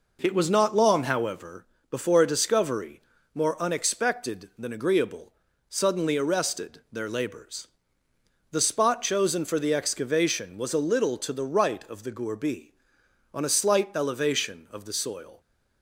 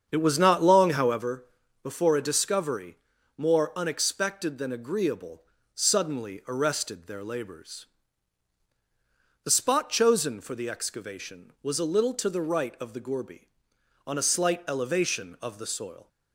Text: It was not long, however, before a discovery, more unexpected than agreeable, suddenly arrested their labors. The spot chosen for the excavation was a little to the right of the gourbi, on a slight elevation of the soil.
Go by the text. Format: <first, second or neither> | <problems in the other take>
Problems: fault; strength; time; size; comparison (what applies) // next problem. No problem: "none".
first | starts louder than the rest; strong; until 1.3 s; 7.5 dB